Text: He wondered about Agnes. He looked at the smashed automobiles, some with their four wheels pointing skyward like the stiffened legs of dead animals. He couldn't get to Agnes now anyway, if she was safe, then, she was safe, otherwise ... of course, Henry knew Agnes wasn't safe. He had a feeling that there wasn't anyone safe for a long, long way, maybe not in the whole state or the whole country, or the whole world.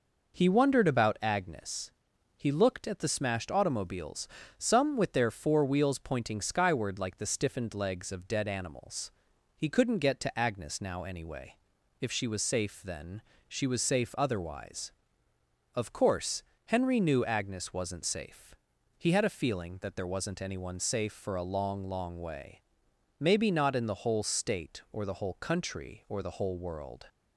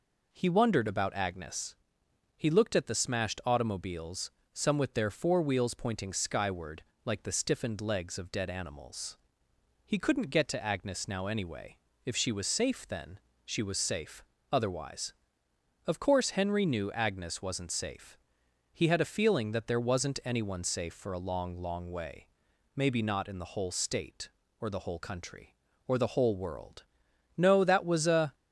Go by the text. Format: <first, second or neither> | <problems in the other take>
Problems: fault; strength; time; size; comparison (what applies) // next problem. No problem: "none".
first | pauses between "skyward" and "like"; slight; at 6.8 s; 0.22 s long // goes on to say "No that was a"; noticeable; from 27.3 s on; 0.98 s long